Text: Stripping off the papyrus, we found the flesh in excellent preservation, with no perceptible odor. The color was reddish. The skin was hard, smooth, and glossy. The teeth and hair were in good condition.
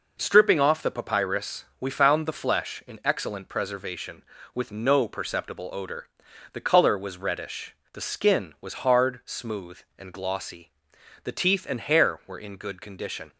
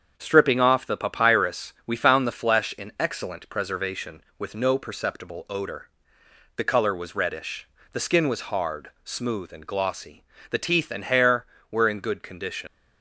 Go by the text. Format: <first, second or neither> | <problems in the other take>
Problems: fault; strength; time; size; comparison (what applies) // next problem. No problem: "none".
first | starts louder than the rest; strong; until 1.1 s; 7.5 dB // leaves "condition" unfinished; at 12.6 s; 100 ms